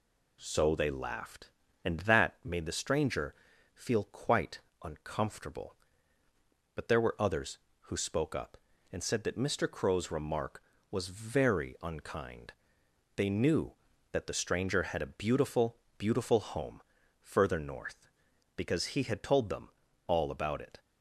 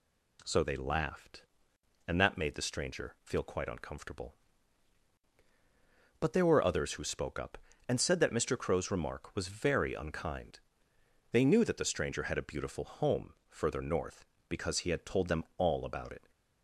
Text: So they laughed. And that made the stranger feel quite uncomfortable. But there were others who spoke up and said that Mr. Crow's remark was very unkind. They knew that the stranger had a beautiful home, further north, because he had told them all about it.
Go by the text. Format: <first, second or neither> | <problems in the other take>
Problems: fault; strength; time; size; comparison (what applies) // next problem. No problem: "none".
second | pauses between "stranger" and "feel"; at 3.3 s; 0.40 s long // pauses between "quite" and "uncomfortable"; slight; at 4.5 s; 0.24 s long // says "beautiful" twice; at 15.9 s // pauses between "them" and "all"; at 19.6 s; 0.40 s long